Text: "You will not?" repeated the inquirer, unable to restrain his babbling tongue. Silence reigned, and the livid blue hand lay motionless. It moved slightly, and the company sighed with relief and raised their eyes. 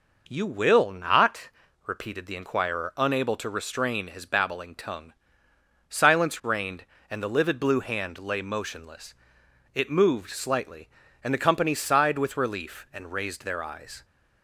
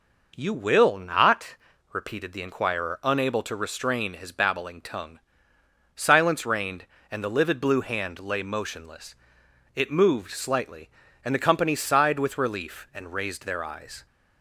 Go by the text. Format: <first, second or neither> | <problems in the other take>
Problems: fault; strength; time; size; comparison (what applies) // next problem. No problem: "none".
neither | none